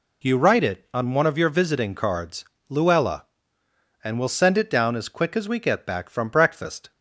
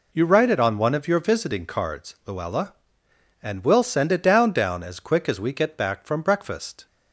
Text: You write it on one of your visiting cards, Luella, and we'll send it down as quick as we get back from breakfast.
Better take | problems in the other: first | says "down" twice; at 4.5 s

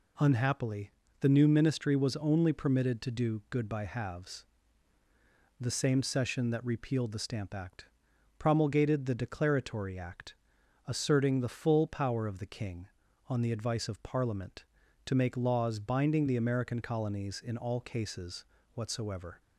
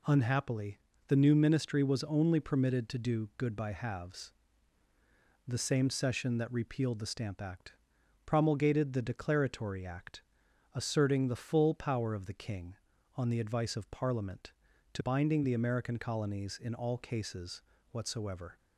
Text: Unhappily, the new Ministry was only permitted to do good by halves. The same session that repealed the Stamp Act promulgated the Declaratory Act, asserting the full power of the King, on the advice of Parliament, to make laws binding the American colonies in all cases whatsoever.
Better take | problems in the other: first | pauses between "Act" and "promulgated"; noticeable; at 7.7 s; 0.52 s long; noticeable in the first // skips "make laws"; at 15.0 s // pauses between "cases" and "whatsoever"; slight; at 17.6 s; 0.30 s long; slight in the first

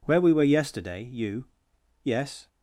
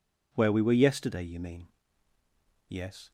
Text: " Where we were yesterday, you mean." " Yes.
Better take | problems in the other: second | skips "mean"; at 1.5 s

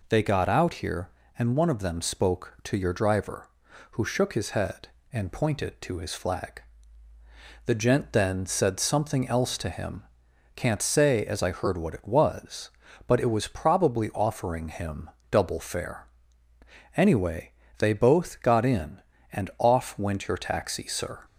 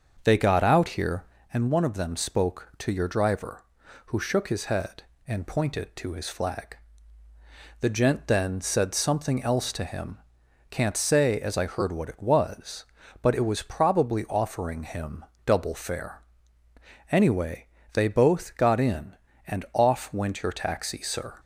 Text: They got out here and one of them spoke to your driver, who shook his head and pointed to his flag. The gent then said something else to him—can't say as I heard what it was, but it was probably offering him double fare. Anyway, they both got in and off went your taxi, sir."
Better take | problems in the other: first | starts louder than the rest; until 1.5 s; 6.5 dB // pauses between "him" and "double"; slight; at 15.2 s; 0.22 s long; slight in the first

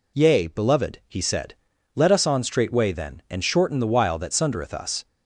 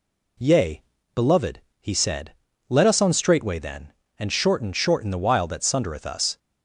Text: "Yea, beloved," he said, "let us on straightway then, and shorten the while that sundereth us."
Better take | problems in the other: first | says "shorten" twice; at 4.7 s

